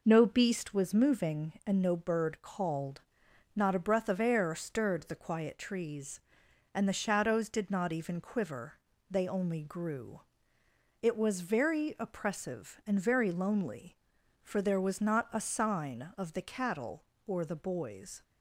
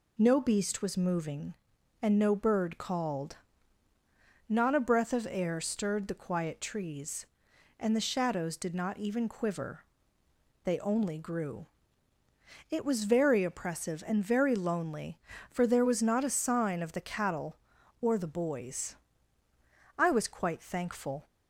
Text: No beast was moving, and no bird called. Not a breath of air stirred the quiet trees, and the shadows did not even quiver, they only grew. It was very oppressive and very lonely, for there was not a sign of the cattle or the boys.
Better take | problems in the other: first | goes on to say "I was quite thankful"; noticeable; from 19.9 s on; 1.3 s long

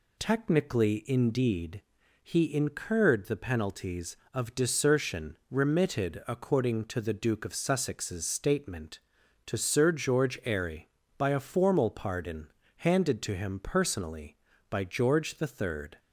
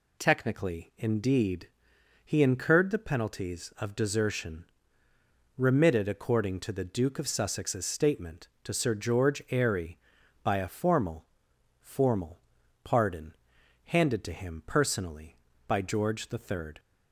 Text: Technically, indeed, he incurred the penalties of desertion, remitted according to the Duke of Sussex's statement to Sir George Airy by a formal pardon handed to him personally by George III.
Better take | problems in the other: first | says "formal" twice; at 11.8 s // pauses between "pardon" and "handed"; noticeable; at 13.3 s; 0.52 s long; slight in the first

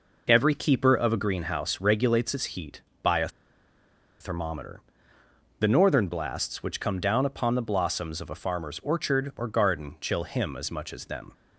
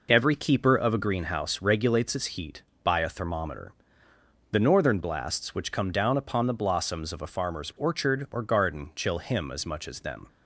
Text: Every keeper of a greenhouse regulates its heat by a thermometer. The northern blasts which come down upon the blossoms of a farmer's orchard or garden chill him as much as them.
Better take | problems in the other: second | pauses between "a" and "thermometer"; noticeable; at 3.2 s; 0.91 s long

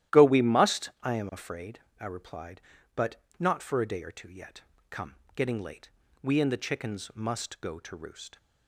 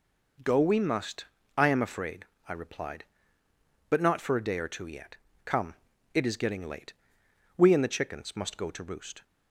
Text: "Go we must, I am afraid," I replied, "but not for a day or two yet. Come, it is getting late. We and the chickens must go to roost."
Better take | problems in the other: second | starts louder than the rest; strong; until 1.2 s; 13 dB // pauses between "but" and "not"; slight; at 3.1 s; 0.20 s long // skips "it is"; at 5.2 s

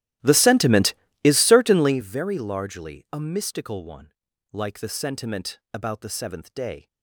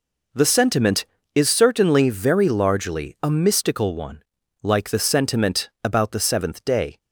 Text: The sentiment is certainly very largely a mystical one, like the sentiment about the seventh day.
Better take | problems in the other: second | starts louder than the rest; strong; until 2.1 s; 14.5 dB

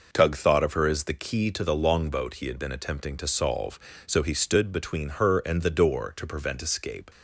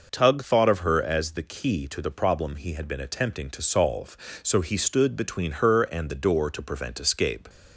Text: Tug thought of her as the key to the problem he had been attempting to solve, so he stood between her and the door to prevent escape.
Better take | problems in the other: second | says "longboat" for "problem"; at 1.7 s

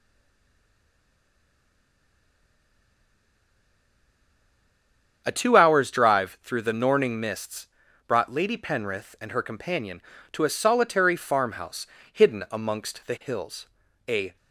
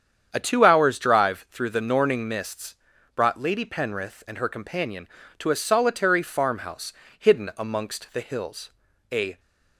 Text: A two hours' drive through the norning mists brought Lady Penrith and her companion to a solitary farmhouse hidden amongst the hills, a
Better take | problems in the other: second | stays silent before the first word; strong; until 5.2 s; 5.2 s long // starts louder than the rest; strong; until 6.2 s; 8 dB; strong in the second // pauses between "mists" and "brought"; at 7.6 s; 0.42 s long; also in the second // pauses between "farmhouse" and "hidden"; slight; at 11.8 s; 0.24 s long; slight in the second

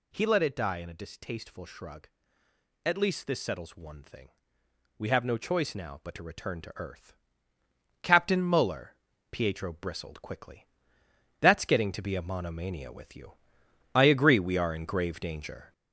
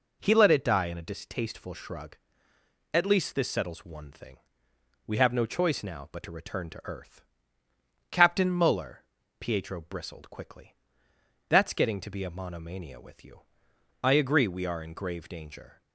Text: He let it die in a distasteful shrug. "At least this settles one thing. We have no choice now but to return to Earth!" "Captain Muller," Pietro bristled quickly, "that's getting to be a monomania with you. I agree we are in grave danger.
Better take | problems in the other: second | gets louder; noticeable; throughout; 4.5 dB

